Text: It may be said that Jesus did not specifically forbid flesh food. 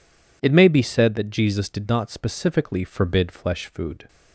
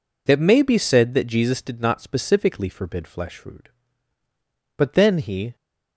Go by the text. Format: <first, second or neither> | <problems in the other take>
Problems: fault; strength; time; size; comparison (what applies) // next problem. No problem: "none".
first | goes on to say "But then he"; noticeable; from 4.7 s on; 0.80 s long